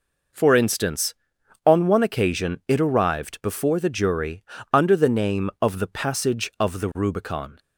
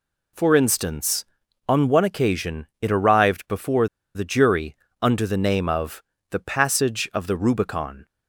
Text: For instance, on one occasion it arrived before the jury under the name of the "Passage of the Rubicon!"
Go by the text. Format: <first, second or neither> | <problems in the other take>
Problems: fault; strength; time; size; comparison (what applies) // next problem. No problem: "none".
first | pauses between "before" and "the"; slight; at 3.8 s; 0.28 s long // pauses between "jury" and "under"; slight; at 4.7 s; 0.26 s long; slight in the first // pauses between "of" and "the"; slight; at 6.0 s; 0.26 s long